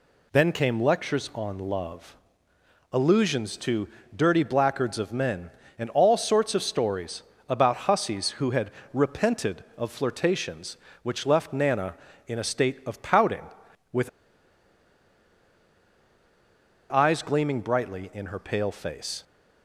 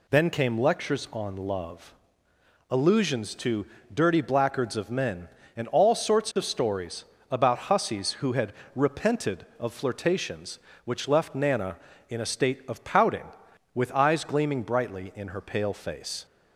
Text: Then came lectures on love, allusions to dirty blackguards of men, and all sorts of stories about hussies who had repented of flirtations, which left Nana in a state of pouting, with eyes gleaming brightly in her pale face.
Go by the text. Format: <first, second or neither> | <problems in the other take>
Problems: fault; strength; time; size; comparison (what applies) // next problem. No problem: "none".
second | pauses between "to" and "dirty"; slight; at 3.8 s; 0.28 s long; slight in the second // pauses between "stories" and "about"; slight; at 7.2 s; 0.24 s long; slight in the second // pauses between "had" and "repented"; slight; at 8.6 s; 0.24 s long; slight in the second // pauses between "with" and "eyes"; strong; at 14.0 s; 2.8 s long